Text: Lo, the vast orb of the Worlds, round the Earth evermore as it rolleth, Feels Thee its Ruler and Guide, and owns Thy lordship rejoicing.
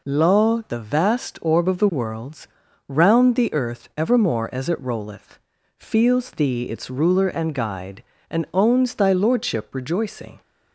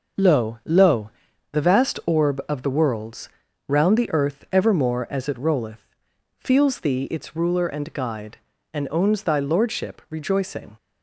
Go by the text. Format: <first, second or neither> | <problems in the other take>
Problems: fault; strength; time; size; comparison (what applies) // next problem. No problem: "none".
first | says "Lo" twice; at 0.6 s